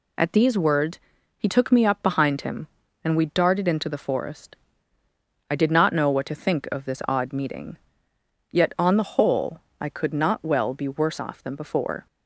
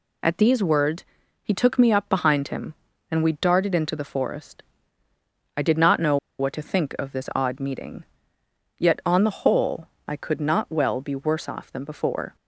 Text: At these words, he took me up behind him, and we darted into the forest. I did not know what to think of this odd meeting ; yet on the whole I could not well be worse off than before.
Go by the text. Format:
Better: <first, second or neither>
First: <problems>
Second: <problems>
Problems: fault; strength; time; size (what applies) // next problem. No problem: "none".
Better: first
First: pauses between "whole" and "I"; slight; at 9.6 s; 0.20 s long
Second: pauses between "know" and "what"; slight; at 6.1 s; 0.22 s long // pauses between "whole" and "I"; slight; at 9.8 s; 0.20 s long